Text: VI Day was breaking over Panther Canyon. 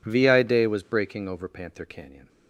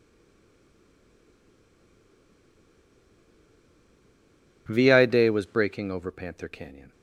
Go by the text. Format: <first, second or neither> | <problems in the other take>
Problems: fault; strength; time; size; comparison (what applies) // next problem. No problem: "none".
first | stays silent before the first word; strong; until 4.6 s; 4.6 s long